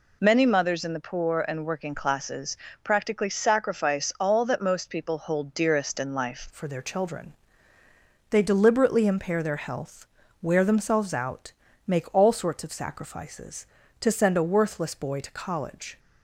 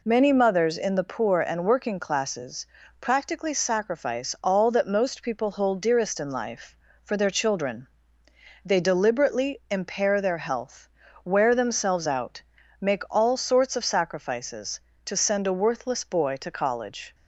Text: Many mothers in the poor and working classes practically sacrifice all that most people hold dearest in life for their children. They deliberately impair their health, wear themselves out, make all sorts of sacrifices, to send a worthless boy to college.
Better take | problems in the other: second | pauses between "classes" and "practically"; slight; at 2.5 s; 0.30 s long; slight in the second // changes voice at "for"; from 6.4 s on; 9.5 s long

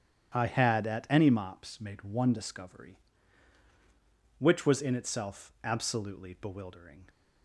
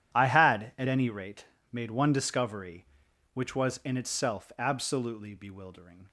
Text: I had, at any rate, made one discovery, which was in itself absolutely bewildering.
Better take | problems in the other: second | starts louder than the rest; strong; until 1.4 s; 10 dB // says "mops" for "rate"; at 1.2 s

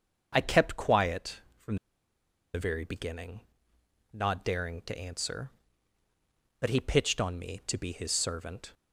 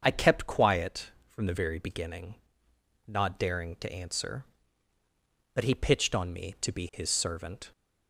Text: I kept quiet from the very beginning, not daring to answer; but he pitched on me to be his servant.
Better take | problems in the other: second | starts louder than the rest; until 1.3 s; 6.5 dB; also in the second // pauses between "from" and "the"; noticeable; at 1.7 s; 0.78 s long

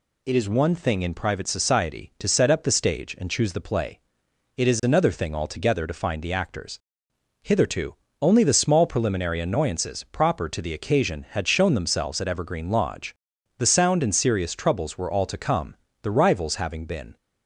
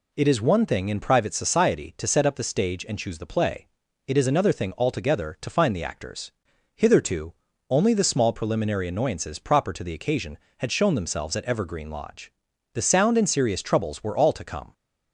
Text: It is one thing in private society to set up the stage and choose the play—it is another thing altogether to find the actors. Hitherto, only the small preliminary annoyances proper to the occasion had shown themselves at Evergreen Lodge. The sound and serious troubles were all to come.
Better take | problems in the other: second | goes on to say "The Rivals having been"; noticeable; from 16.0 s on; 1.1 s long

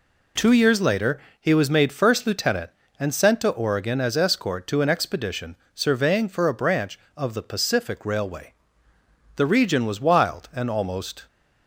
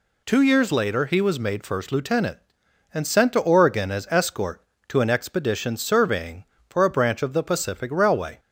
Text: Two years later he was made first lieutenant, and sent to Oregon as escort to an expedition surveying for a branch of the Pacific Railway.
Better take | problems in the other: second | pauses between "later" and "he"; slight; at 1.1 s; 0.22 s long // pauses between "expedition" and "surveying"; slight; at 5.5 s; 0.20 s long // goes on to say "The region was wild and almost"; strong; from 9.3 s on; 1.9 s long

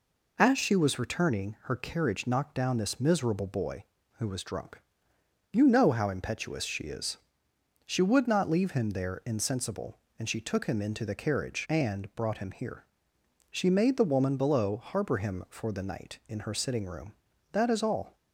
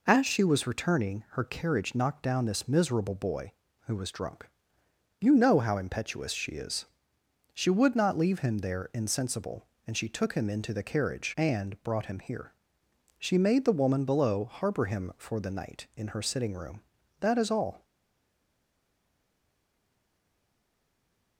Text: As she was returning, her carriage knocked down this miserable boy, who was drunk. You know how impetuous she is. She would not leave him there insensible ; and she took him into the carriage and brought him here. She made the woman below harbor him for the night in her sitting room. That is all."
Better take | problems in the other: first | stays silent after the last word; strong; from 17.8 s on; 3.5 s long

